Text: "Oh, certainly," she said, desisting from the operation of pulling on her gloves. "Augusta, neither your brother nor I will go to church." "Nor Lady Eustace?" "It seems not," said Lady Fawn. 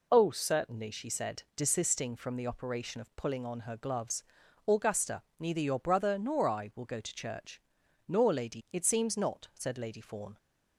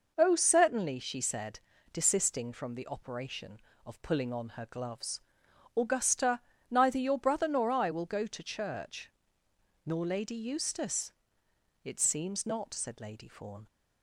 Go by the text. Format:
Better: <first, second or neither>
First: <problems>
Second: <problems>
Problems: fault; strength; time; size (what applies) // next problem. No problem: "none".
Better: second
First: skips "Eustace"; at 8.6 s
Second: none